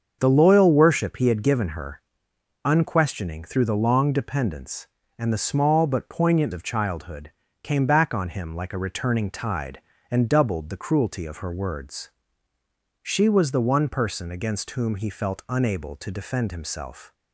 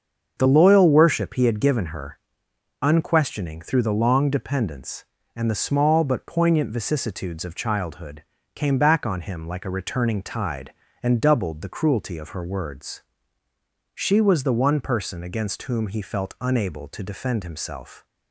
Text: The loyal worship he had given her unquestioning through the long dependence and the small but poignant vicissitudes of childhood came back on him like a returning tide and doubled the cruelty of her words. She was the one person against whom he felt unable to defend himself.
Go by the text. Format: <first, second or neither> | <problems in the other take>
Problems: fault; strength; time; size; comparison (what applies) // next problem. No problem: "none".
second | starts louder than the rest; until 1.2 s; 6.5 dB; also in the second // pauses between "her" and "unquestioning"; noticeable; at 2.0 s; 0.64 s long; noticeable in the second // skips "vicissitudes"; at 6.5 s // pauses between "childhood" and "came"; slight; at 7.2 s; 0.32 s long; slight in the second